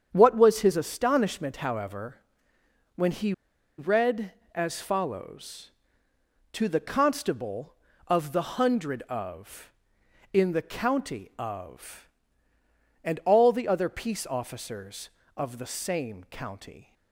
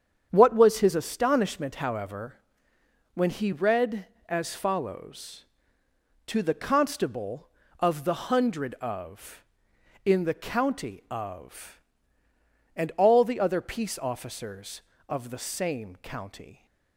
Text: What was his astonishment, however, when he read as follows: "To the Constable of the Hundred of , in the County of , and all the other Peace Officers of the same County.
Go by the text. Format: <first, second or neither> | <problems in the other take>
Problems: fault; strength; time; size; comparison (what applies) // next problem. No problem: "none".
second | starts louder than the rest; strong; until 1.1 s; 8 dB; strong in the second // pauses between "he" and "read"; noticeable; at 3.3 s; 0.46 s long